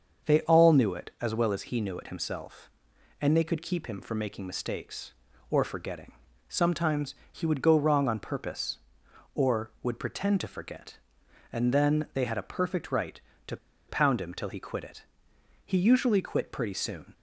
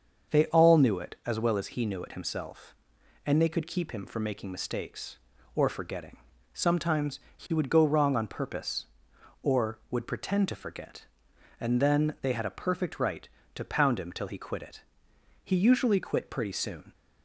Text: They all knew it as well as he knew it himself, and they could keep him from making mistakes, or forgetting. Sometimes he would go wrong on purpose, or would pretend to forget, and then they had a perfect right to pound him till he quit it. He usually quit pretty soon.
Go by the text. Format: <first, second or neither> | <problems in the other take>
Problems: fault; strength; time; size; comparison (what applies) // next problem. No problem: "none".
second | starts louder than the rest; until 1.3 s; 6.5 dB; also in the second // pauses between "Sometimes" and "he"; slight; at 7.1 s; 0.16 s long; slight in the second // pauses between "to" and "pound"; slight; at 13.5 s; 0.31 s long